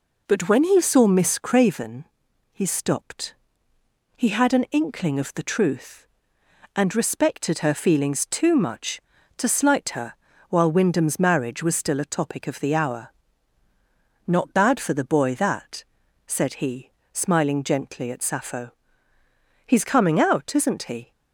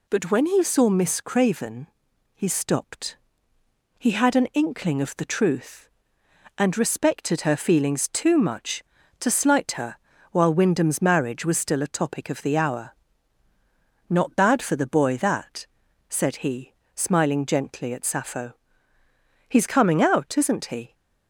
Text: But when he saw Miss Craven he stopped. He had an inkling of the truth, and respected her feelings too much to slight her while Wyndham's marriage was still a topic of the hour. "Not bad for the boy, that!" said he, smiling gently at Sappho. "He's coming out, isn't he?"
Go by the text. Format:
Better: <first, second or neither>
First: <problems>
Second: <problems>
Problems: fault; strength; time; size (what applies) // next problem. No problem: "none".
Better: second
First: starts louder than the rest; noticeable; until 1.9 s; 4 dB // pauses between "Craven" and "he"; noticeable; at 2.0 s; 0.46 s long // pauses between "her" and "while"; slight; at 10.1 s; 0.36 s long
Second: pauses between "Craven" and "he"; noticeable; at 1.8 s; 0.46 s long // pauses between "her" and "while"; slight; at 9.9 s; 0.36 s long